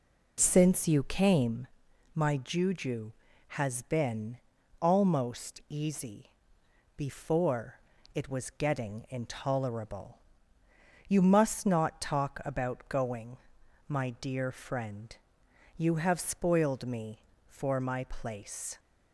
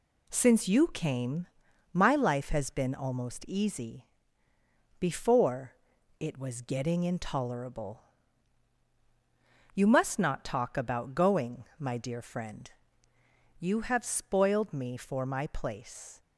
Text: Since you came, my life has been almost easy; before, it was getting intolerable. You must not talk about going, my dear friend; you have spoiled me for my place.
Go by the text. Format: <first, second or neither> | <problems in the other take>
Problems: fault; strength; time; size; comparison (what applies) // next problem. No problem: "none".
second | says "juju" for "life"; at 2.3 s // pauses between "been" and "almost"; at 4.3 s; 0.44 s long